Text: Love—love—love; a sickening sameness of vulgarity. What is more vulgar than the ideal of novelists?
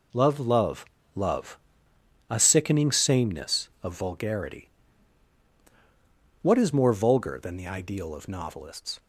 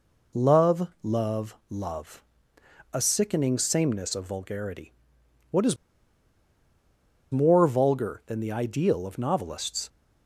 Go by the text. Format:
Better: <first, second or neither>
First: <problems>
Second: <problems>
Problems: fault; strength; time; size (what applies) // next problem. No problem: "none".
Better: first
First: none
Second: pauses between "is" and "more"; strong; at 5.7 s; 1.5 s long